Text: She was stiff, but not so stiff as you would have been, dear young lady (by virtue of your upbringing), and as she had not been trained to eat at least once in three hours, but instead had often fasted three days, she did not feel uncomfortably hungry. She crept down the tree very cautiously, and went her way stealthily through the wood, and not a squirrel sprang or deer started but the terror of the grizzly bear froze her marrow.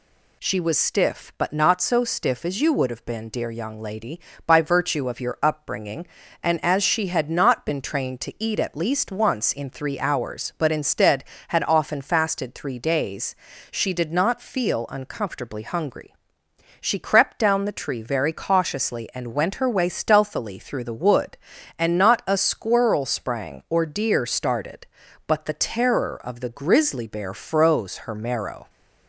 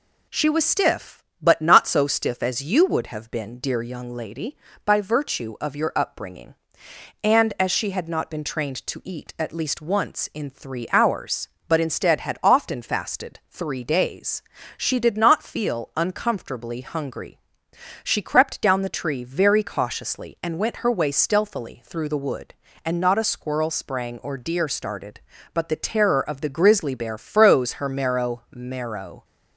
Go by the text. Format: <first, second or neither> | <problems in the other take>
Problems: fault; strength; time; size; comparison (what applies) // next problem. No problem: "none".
first | says "marrow" twice; at 28.5 s